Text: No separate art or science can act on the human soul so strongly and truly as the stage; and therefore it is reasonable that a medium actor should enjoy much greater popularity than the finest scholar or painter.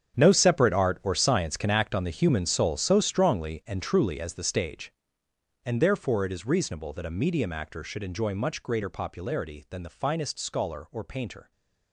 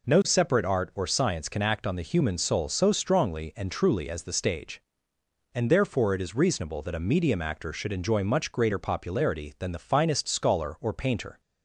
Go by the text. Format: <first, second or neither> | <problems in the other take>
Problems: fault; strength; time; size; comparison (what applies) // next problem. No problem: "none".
second | gets quieter; strong; throughout; 14.5 dB